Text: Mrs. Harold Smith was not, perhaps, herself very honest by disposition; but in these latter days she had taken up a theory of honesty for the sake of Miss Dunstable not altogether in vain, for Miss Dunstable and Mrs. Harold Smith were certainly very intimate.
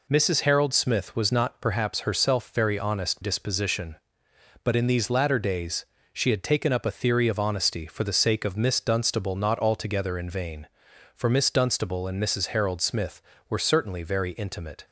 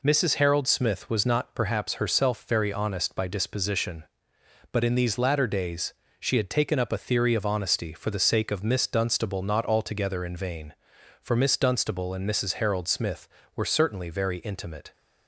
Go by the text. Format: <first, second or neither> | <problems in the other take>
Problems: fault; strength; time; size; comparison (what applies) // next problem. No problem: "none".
second | skips "by"; at 3.2 s // pauses between "days" and "she"; slight; at 5.8 s; 0.26 s long; slight in the second